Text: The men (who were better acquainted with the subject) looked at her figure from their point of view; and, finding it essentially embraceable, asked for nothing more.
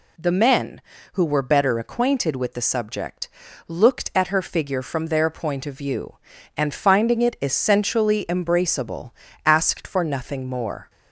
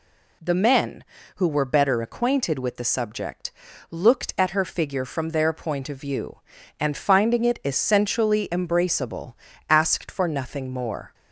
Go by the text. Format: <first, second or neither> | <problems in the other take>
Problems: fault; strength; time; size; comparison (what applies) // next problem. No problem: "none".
neither | none